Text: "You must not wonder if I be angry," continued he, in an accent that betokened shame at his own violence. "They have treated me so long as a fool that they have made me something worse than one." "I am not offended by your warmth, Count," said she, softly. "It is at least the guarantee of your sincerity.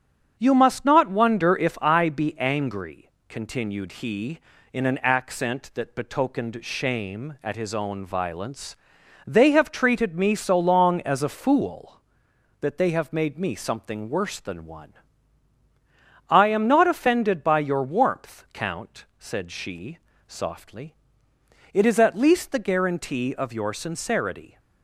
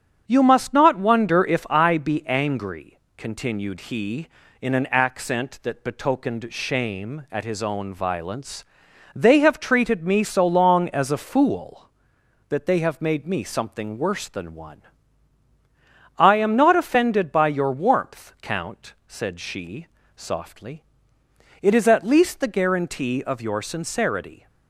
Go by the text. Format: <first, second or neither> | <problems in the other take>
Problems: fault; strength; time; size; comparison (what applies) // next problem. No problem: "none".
neither | starts louder than the rest; strong; the same in both